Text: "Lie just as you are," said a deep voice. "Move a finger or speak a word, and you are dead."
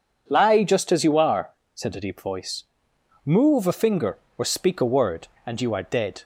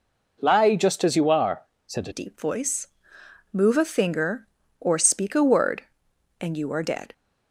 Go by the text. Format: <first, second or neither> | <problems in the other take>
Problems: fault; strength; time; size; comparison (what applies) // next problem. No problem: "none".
first | changes voice at "deep"; from 2.1 s on; 5.0 s long